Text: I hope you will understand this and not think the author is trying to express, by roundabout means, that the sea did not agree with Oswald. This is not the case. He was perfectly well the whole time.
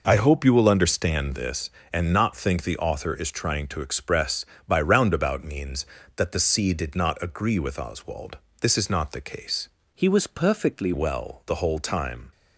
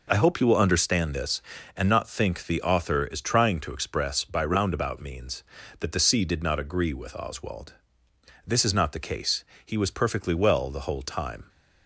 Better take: second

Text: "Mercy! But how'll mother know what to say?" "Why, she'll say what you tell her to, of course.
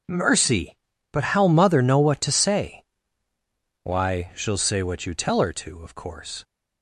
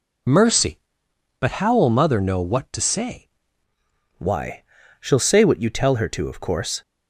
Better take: first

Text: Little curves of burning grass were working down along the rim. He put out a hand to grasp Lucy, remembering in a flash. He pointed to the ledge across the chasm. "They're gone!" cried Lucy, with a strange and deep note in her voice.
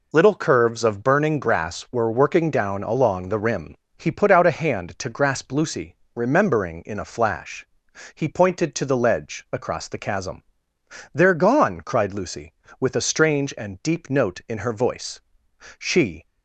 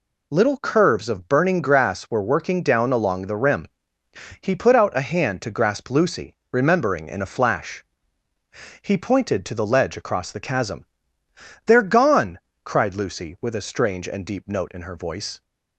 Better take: second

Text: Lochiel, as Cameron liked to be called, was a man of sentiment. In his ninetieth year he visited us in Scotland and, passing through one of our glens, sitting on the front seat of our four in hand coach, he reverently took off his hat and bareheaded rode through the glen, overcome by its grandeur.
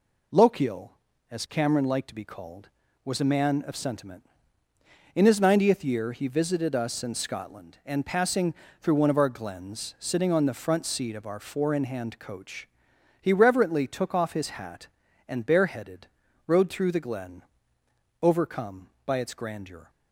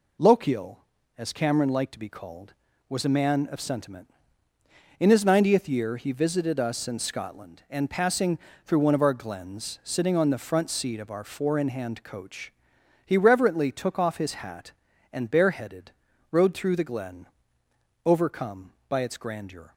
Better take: neither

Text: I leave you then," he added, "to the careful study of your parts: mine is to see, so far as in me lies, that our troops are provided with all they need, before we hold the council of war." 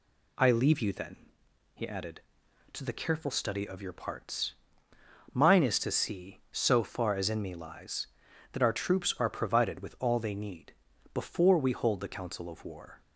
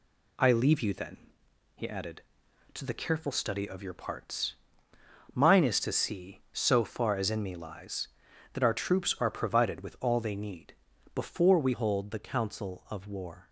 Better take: first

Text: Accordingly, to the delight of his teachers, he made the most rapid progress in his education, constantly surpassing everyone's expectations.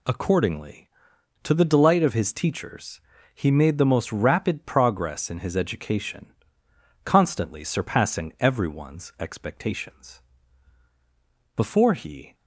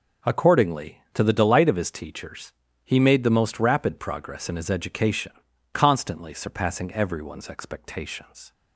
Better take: second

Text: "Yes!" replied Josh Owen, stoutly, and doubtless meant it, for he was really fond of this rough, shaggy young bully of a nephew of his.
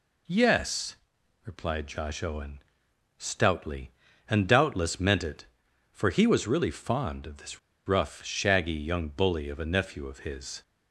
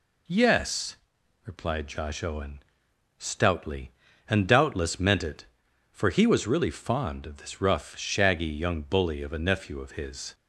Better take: second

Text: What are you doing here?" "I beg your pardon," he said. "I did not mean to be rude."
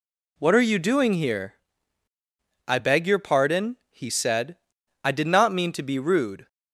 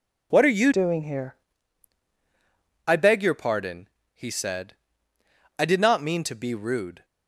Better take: first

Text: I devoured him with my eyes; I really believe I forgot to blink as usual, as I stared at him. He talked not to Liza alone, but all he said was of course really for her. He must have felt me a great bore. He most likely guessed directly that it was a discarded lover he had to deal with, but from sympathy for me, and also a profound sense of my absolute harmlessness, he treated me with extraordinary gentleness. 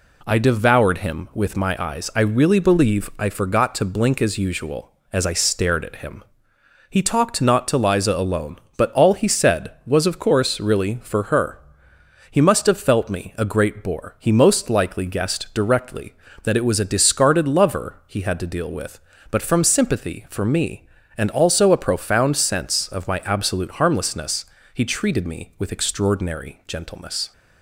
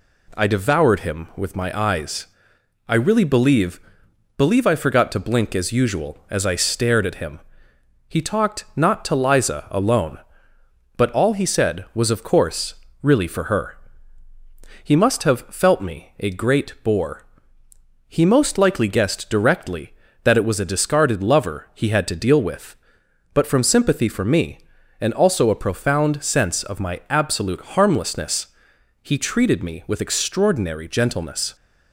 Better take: first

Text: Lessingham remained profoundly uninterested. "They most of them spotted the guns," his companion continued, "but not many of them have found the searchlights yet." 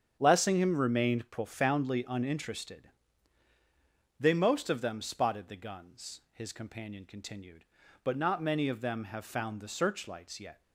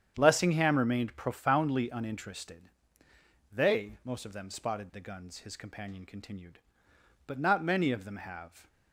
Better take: first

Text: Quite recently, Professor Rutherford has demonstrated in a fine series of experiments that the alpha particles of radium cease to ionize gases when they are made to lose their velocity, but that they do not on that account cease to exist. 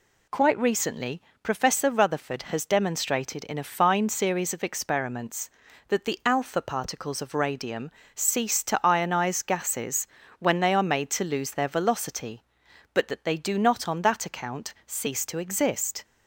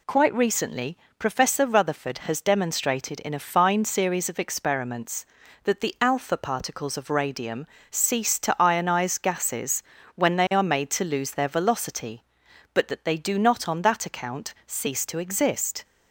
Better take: neither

